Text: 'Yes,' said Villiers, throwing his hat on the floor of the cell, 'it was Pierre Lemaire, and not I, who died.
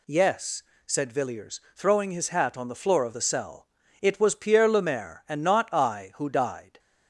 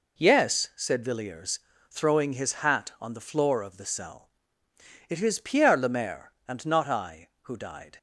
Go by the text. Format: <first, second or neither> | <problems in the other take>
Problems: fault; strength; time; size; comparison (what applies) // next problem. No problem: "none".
first | says "is" for "was"; at 5.2 s